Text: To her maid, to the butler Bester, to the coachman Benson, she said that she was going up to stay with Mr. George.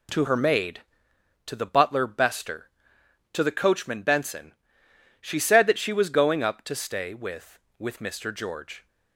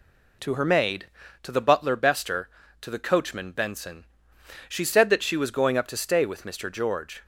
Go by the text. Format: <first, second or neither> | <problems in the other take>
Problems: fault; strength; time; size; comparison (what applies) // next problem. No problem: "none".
second | says "with" twice; at 7.7 s